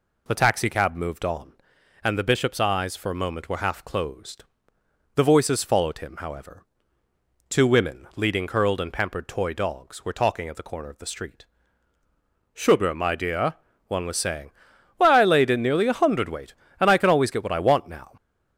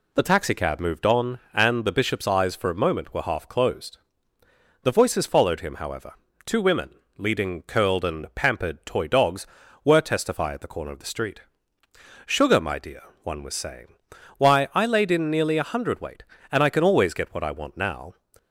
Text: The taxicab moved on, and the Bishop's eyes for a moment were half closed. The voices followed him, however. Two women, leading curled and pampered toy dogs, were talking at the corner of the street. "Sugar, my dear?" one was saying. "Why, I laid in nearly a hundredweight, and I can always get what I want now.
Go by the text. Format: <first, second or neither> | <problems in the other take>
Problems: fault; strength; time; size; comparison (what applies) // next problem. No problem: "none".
first | says "testify" for "talking"; at 10.0 s